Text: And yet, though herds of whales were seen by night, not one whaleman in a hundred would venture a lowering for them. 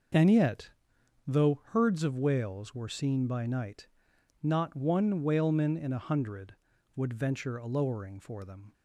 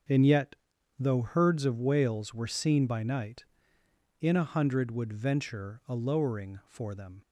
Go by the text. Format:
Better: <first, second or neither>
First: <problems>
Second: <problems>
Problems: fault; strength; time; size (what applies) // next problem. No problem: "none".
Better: first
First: starts louder than the rest; until 1.8 s; 6 dB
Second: starts louder than the rest; until 1.5 s; 7 dB // skips "not one whaleman"; at 3.8 s